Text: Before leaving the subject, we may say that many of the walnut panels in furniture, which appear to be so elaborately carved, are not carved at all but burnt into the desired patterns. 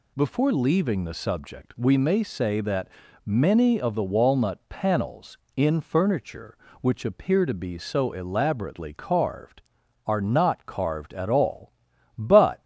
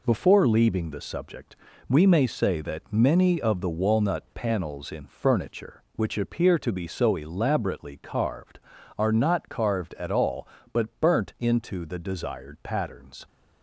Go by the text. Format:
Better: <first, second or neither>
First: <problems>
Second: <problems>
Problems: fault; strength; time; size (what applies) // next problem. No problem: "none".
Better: second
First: pauses between "that" and "many"; slight; at 2.8 s; 0.36 s long // stops before "burnt into the desired patterns"; at 12.5 s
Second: none